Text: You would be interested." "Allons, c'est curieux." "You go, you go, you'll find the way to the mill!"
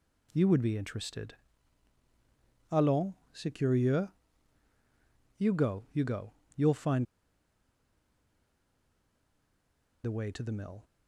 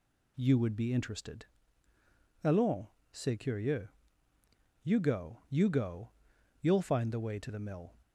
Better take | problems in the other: second | pauses between "find" and "the"; strong; at 7.0 s; 3.0 s long

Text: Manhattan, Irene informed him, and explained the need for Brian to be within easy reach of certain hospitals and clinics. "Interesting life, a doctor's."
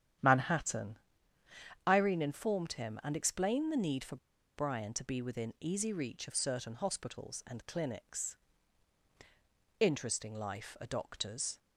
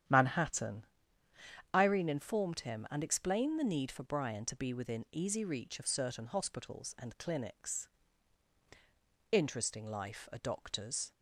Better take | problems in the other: second | starts louder than the rest; strong; until 2.0 s; 10 dB; strong in the second // pauses between "for" and "Brian"; at 4.1 s; 0.38 s long

